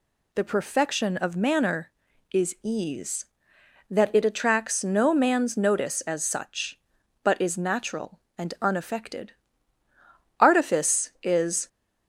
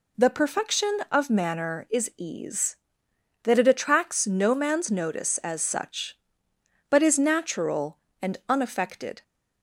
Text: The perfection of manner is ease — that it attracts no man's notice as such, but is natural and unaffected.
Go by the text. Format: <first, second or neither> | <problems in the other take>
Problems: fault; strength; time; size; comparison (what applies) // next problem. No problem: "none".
second | goes on to say "Artifice is"; noticeable; from 10.3 s on; 1.2 s long